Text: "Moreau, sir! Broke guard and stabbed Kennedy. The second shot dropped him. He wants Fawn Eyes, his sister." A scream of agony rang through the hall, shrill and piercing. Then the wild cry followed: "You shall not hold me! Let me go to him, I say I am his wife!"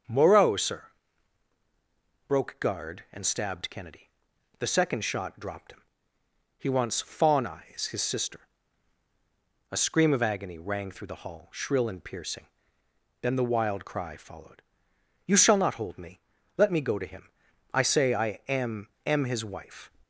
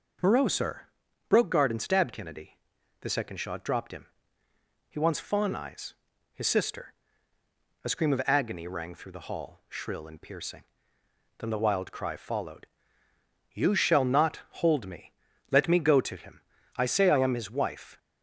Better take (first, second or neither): second